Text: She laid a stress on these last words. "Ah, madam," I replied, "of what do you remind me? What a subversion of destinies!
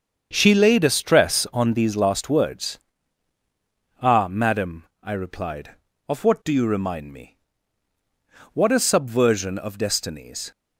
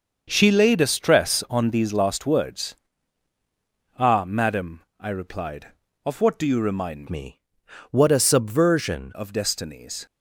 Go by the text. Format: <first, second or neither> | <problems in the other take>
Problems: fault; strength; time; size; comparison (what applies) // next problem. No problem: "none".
first | starts louder than the rest; until 1.3 s; 6 dB; also in the first // changes voice from "me" to "subversion"; from 7.0 to 9.1 s; 2.1 s long